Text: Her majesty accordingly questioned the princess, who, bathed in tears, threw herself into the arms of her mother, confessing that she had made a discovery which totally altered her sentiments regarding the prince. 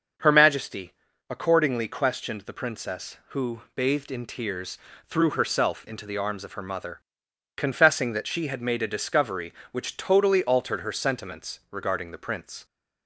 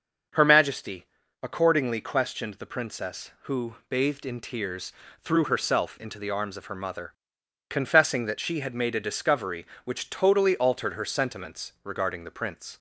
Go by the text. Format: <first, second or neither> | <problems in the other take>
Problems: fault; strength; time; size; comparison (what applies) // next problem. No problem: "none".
neither | starts louder than the rest; the same in both // pauses between "majesty" and "accordingly"; slight; the same in both